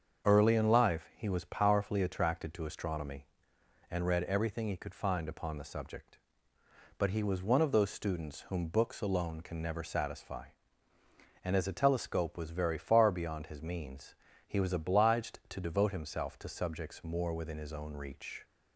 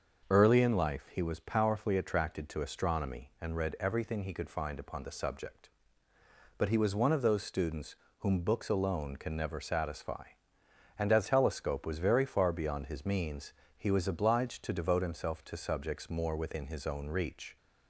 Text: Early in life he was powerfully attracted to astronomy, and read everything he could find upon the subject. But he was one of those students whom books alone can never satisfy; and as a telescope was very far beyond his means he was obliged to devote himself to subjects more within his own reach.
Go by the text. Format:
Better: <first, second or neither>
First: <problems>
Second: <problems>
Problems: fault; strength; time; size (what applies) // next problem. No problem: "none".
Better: first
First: starts louder than the rest; until 1.3 s; 7 dB // pauses between "means" and "he"; slight; at 14.1 s; 0.32 s long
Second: starts louder than the rest; until 1.3 s; 6.5 dB // pauses between "students" and "whom"; slight; at 7.9 s; 0.24 s long // skips "a"; at 11.2 s // pauses between "means" and "he"; slight; at 13.5 s; 0.24 s long